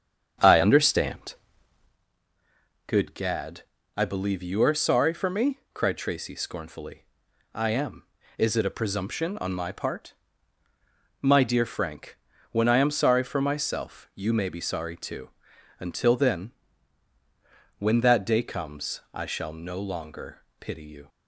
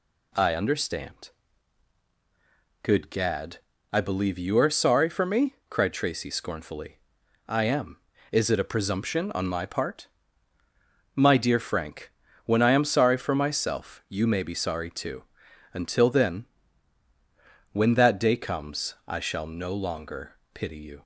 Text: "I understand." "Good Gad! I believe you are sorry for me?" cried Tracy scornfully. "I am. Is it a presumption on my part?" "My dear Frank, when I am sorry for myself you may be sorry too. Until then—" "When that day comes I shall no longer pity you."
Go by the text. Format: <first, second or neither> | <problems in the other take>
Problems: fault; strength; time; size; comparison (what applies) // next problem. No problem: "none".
second | starts louder than the rest; strong; until 2.0 s; 8 dB // pauses between "longer" and "pity"; slight; at 20.4 s; 0.18 s long; slight in the second